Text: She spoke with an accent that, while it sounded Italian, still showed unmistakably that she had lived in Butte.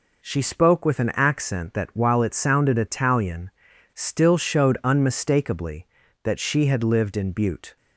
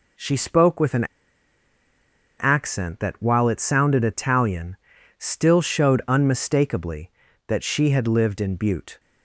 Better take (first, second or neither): first